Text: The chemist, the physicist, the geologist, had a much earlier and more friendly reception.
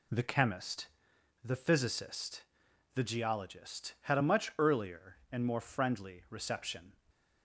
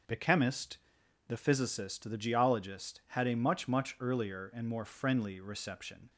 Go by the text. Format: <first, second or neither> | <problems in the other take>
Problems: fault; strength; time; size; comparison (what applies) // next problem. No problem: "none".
first | starts louder than the rest; until 1.5 s; 6.5 dB // says "much" twice; at 3.6 s